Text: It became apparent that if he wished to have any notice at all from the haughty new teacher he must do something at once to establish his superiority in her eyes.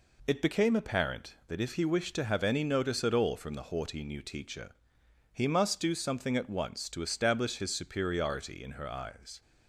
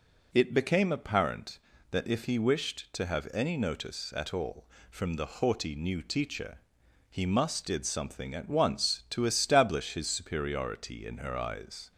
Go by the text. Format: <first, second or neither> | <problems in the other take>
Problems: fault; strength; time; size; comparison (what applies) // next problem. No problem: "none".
first | pauses between "teacher" and "he"; noticeable; at 6.5 s; 0.52 s long; noticeable in the first // says "did" for "do"; at 7.6 s